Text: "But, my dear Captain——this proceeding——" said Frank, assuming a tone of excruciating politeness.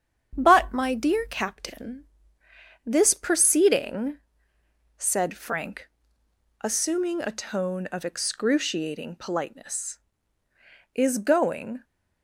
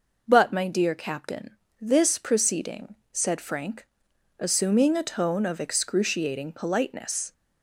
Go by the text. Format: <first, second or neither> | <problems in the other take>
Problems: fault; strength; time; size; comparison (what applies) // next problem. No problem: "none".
second | starts louder than the rest; strong; until 1.3 s; 8 dB // goes on to say "Is going"; noticeable; from 10.9 s on; 0.88 s long